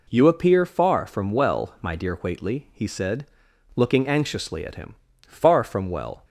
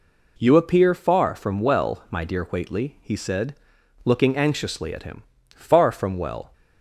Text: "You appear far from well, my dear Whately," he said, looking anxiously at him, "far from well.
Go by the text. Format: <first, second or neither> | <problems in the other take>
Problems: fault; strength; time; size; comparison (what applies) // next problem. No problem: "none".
neither | none